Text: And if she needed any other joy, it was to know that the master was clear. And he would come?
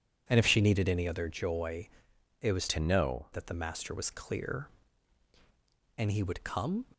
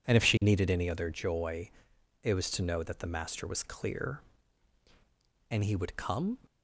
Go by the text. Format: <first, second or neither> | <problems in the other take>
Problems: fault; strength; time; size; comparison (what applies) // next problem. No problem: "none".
second | changes voice from "to" to "know"; from 2.6 to 3.2 s; 0.6 s long